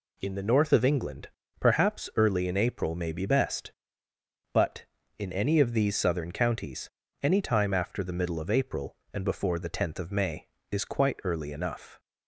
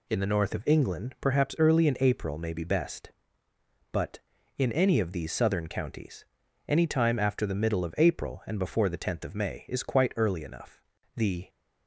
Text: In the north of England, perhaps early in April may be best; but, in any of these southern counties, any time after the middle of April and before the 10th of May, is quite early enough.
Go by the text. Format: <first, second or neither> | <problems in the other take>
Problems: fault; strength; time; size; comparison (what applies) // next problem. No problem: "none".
first | goes on to say "The"; slight; from 11.1 s on; 0.34 s long